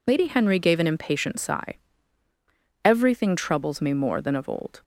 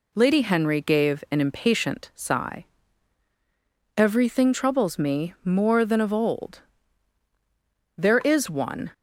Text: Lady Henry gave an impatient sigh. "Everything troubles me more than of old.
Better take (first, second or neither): first